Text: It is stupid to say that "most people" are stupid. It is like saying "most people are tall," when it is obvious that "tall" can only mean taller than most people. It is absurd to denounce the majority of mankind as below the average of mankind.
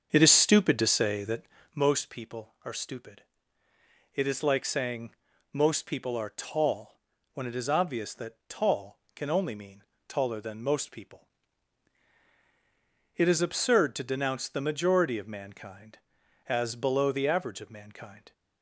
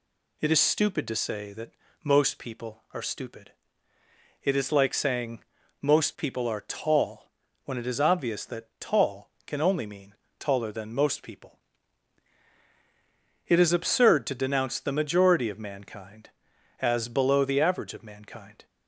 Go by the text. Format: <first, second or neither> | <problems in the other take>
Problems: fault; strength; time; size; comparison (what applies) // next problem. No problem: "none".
second | starts louder than the rest; until 1.8 s; 7 dB // pauses between "that" and "most"; slight; at 1.4 s; 0.32 s long; slight in the second // pauses between "saying" and "most"; slight; at 5.1 s; 0.36 s long; slight in the second // pauses between "mean" and "taller"; slight; at 9.8 s; 0.24 s long; slight in the second